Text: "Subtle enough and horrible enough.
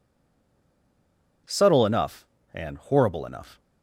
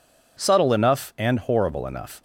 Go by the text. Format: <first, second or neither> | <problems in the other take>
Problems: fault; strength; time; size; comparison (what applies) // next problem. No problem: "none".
second | stays silent before the first word; noticeable; until 1.4 s; 1.4 s long